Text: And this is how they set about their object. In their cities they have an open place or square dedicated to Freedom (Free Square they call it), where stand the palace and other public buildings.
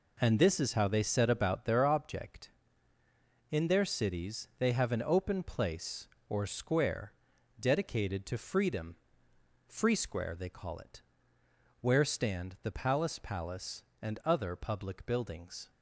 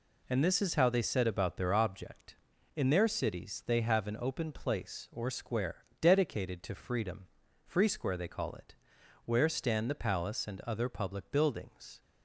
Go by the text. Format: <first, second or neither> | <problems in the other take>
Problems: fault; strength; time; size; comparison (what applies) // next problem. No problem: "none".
second | pauses between "square" and "dedicated"; noticeable; at 7.1 s; 0.48 s long; slight in the second // says "palace" twice; at 13.2 s